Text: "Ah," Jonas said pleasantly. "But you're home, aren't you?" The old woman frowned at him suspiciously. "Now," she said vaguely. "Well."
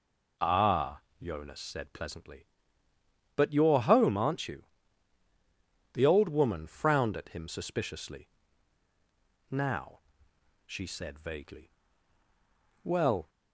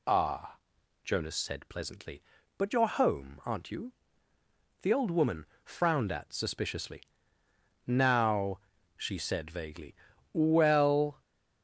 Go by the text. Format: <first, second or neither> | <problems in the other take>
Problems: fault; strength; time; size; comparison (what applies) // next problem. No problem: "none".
first | pauses between "woman" and "frowned"; slight; at 5.4 s; 0.18 s long // skips "him"; at 6.3 s